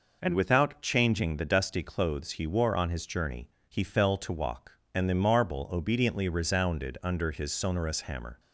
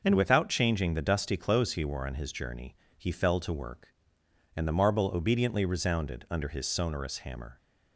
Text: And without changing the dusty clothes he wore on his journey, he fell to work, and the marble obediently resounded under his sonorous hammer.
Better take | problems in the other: second | says "walk" for "work"; at 4.3 s

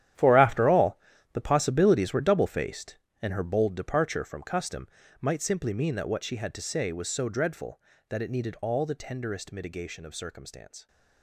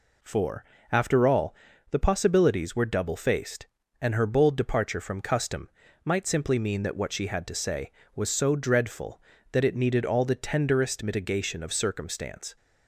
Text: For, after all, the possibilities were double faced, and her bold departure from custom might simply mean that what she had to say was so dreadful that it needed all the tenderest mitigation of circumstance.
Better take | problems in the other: second | gets quieter; strong; throughout; 14 dB // pauses between "custom" and "might"; slight; at 4.8 s; 0.31 s long; slight in the second

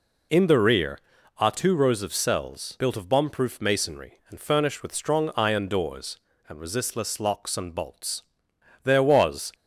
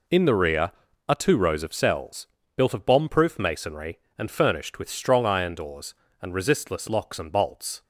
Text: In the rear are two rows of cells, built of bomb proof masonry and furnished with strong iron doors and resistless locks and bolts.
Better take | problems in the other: second | goes on to say "There was"; noticeable; from 8.8 s on; 0.68 s long

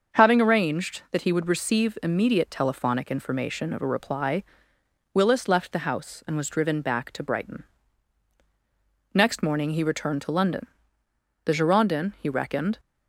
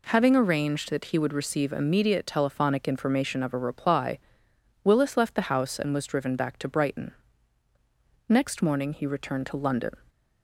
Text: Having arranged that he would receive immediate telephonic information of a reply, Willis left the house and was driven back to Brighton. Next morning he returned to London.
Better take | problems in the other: second | starts louder than the rest; until 1.2 s; 6.5 dB // goes on to say "The Girondin he reckoned"; from 11.4 s on; 1.3 s long

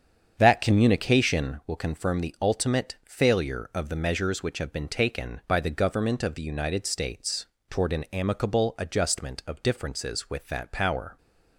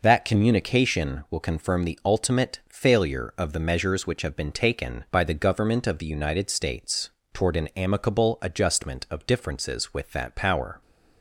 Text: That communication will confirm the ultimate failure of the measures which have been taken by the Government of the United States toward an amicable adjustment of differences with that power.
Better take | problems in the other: second | starts louder than the rest; strong; until 1.5 s; 7.5 dB // pauses between "States" and "toward"; slight; at 7.4 s; 0.24 s long; slight in the second

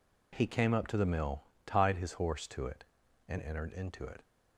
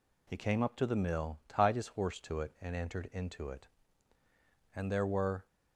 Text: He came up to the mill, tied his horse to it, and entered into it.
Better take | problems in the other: first | goes on to say "And there were"; noticeable; from 4.7 s on; 0.72 s long

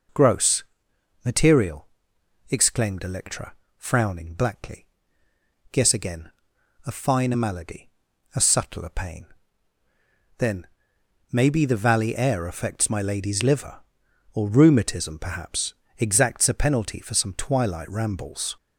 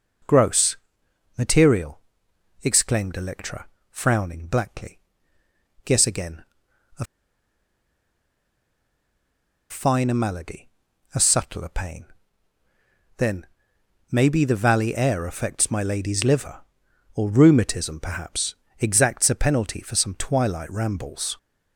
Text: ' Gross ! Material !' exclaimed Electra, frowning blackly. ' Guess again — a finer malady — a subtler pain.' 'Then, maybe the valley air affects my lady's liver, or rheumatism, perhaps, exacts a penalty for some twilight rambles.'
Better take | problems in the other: first | pauses between "a" and "finer"; strong; at 7.0 s; 2.6 s long

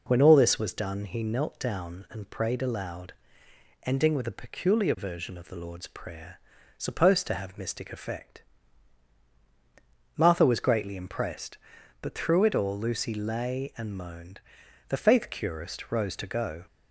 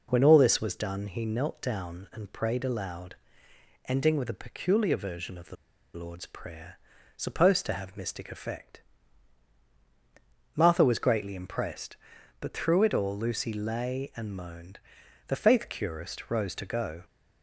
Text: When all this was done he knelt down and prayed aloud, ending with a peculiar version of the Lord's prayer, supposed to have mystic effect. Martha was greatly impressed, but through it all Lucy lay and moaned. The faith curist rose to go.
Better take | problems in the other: first | pauses between "the" and "Lord's"; at 5.5 s; 0.38 s long

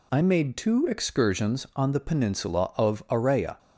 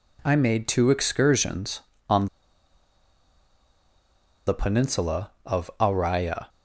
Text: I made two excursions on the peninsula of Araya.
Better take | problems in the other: first | pauses between "on" and "the"; strong; at 2.2 s; 2.2 s long

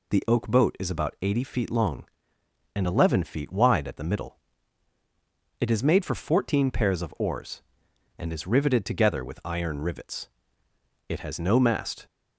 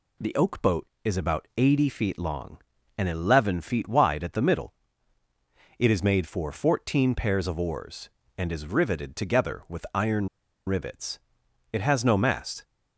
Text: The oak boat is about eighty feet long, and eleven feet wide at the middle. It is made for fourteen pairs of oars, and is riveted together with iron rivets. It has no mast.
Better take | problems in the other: first | pauses between "iron" and "rivets"; at 10.2 s; 0.39 s long

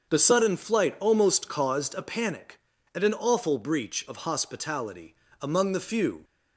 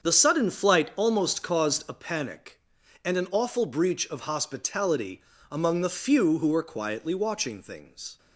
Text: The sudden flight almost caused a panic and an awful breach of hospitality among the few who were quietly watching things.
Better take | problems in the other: second | starts louder than the rest; until 1.1 s; 6.5 dB; strong in the second // pauses between "hospitality" and "among"; slight; at 5.1 s; 0.26 s long; slight in the second // stops before "who were quietly watching things"; at 6.2 s

